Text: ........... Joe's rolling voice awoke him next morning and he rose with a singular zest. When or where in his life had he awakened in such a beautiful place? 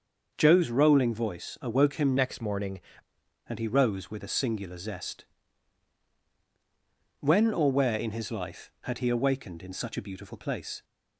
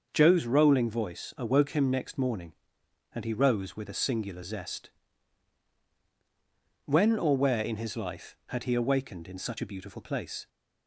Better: second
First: starts louder than the rest; until 1.3 s; 6.5 dB // changes voice from "next" to "morning"; from 2.1 to 2.8 s; 0.7 s long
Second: starts louder than the rest; until 1.1 s; 6.5 dB

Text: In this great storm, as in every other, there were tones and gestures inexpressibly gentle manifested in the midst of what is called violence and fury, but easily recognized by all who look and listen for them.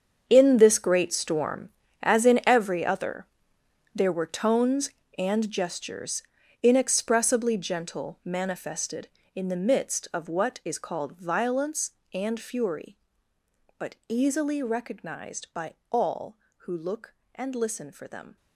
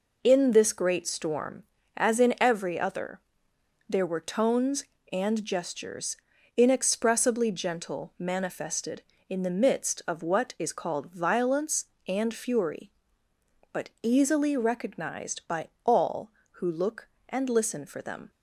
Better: second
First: gets quieter; strong; throughout; 13.5 dB // pauses between "gestures" and "inexpressibly"; at 6.2 s; 0.40 s long // pauses between "by" and "all"; slight; at 15.7 s; 0.18 s long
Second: pauses between "gestures" and "inexpressibly"; at 6.1 s; 0.40 s long // pauses between "by" and "all"; slight; at 15.6 s; 0.18 s long

